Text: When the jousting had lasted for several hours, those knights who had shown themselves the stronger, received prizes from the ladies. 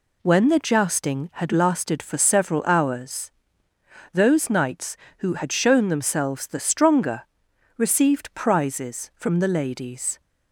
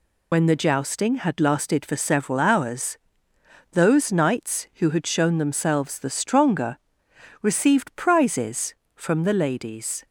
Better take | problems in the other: first | loses the start of "When"; at 0.3 s; 65 ms

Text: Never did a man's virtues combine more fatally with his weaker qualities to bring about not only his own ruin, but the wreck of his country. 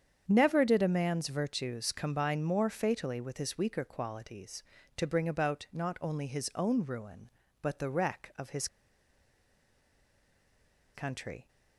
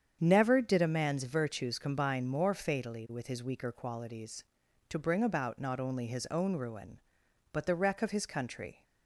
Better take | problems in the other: second | starts louder than the rest; strong; until 1.2 s; 8 dB; strong in the second // pauses between "his" and "country"; strong; at 8.6 s; 2.2 s long

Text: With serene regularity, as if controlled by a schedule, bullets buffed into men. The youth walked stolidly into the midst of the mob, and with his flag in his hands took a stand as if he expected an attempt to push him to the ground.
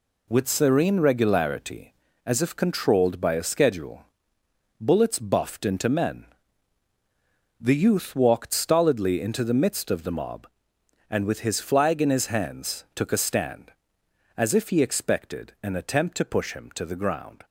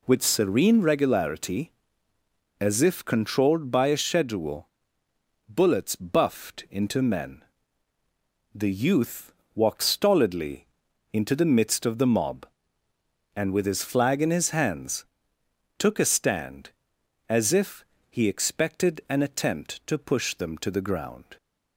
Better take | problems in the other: first | pauses between "youth" and "walked"; slight; at 9.3 s; 0.24 s long // pauses between "stolidly" and "into"; noticeable; at 10.6 s; 0.46 s long // pauses between "hands" and "took"; noticeable; at 15.0 s; 0.74 s long // pauses between "if" and "he"; slight; at 17.8 s; 0.26 s long // says "them" for "him"; at 20.3 s

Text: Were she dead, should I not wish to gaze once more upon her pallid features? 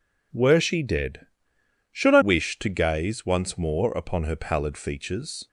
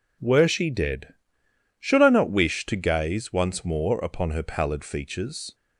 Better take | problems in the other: second | skips "not"; at 2.2 s

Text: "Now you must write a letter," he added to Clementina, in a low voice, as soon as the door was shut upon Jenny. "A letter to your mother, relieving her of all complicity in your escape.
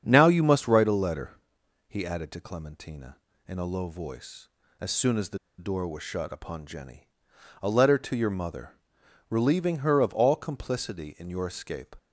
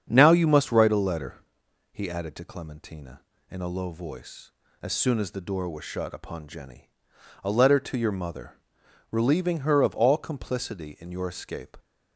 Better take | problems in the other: second | starts louder than the rest; strong; until 1.0 s; 7.5 dB; strong in the second // pauses between "the" and "door"; slight; at 5.3 s; 0.20 s long

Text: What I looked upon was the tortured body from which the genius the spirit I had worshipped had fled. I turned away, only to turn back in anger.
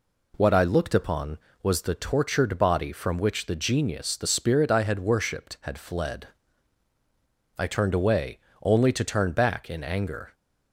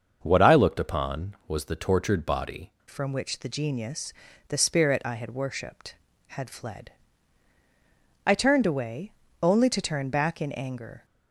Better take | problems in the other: first | starts louder than the rest; until 1.2 s; 6.5 dB // changes voice at "from"; from 2.8 s on; 8.2 s long // pauses between "genius" and "the"; slight; at 4.1 s; 0.36 s long

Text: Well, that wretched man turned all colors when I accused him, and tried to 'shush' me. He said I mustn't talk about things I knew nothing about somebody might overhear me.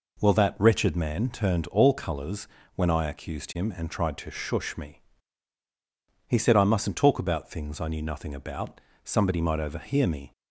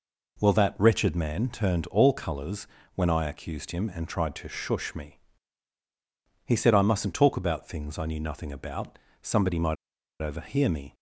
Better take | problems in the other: first | pauses between "colors" and "when"; slight; at 2.6 s; 0.26 s long; slight in the first // pauses between "about" and "somebody"; slight; at 8.9 s; 0.24 s long; slight in the first // pauses between "might" and "overhear"; noticeable; at 9.7 s; 0.46 s long

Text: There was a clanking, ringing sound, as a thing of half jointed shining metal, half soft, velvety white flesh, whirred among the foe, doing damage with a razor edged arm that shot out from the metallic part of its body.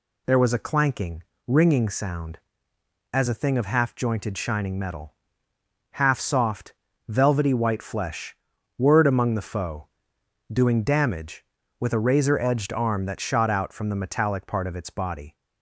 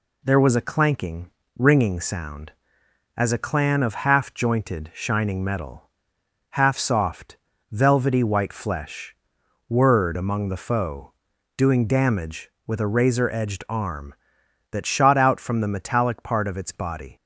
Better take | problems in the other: first | says "clan" for "thing"; at 3.3 s

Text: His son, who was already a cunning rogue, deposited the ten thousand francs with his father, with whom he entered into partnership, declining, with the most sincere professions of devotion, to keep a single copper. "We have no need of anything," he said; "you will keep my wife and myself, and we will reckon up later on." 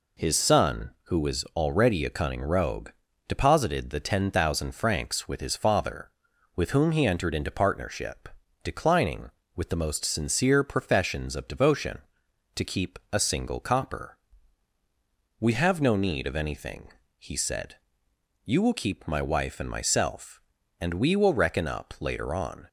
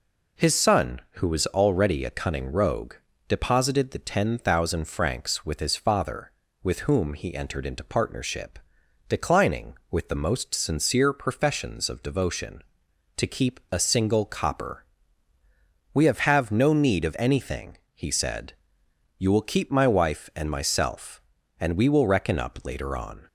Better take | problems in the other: first | says "have" twice; at 16.1 s

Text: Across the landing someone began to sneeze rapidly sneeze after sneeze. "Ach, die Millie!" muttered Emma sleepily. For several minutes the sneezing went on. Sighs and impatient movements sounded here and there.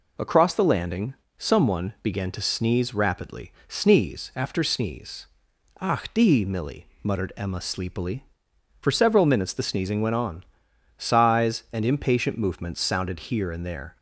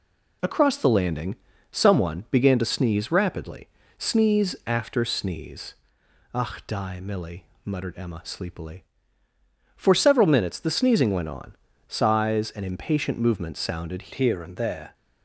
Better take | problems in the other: first | pauses between "landing" and "someone"; slight; at 1.3 s; 0.36 s long; slight in the first // pauses between "rapidly" and "sneeze"; slight; at 3.6 s; 0.30 s long // changes voice at "here"; from 14.1 s on; 0.8 s long

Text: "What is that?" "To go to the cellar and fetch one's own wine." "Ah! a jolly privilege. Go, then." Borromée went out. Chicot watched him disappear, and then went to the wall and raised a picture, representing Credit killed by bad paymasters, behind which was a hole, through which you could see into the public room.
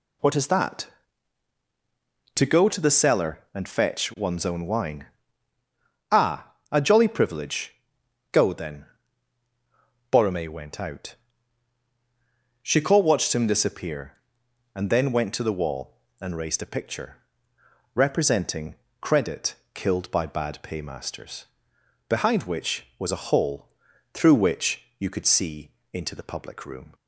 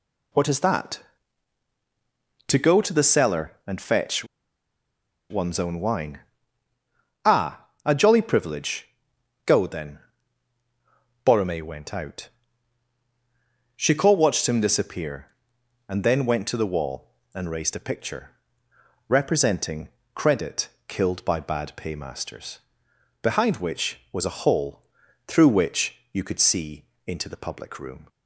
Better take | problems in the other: first | pauses between "fetch" and "one's"; at 4.2 s; 1.0 s long // pauses between "representing" and "Credit"; slight; at 19.8 s; 0.26 s long; slight in the first // pauses between "Credit" and "killed"; slight; at 20.6 s; 0.18 s long; slight in the first // pauses between "which" and "you"; slight; at 25.9 s; 0.16 s long; slight in the first // pauses between "see" and "into"; slight; at 26.8 s; 0.20 s long; slight in the first

